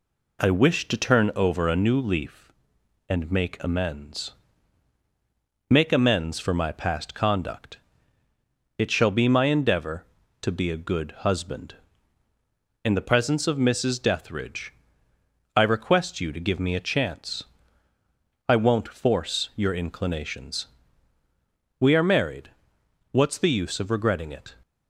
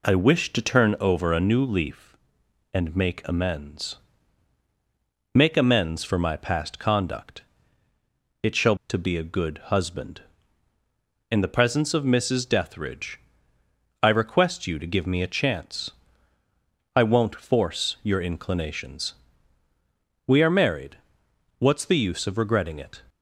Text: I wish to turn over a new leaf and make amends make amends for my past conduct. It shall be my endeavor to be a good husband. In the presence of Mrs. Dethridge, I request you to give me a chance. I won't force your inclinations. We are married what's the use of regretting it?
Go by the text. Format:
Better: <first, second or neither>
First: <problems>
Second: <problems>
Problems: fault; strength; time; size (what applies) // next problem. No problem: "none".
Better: first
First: pauses between "amends" and "make"; strong; at 4.3 s; 1.3 s long // pauses between "married" and "what's"; noticeable; at 22.4 s; 0.62 s long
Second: pauses between "amends" and "make"; strong; at 3.9 s; 1.3 s long // skips "be my endeavor"; at 8.8 s // pauses between "married" and "what's"; noticeable; at 20.9 s; 0.62 s long